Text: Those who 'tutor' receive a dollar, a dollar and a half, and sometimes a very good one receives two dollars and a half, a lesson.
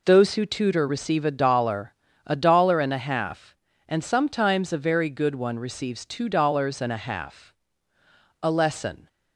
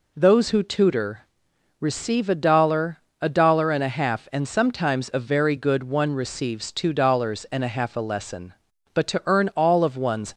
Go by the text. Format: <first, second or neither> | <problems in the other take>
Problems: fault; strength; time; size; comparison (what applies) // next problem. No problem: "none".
first | pauses between "tutor" and "receive"; noticeable; at 1.2 s; 0.54 s long // goes on to say "But to earn all of one's"; from 8.9 s on; 1.3 s long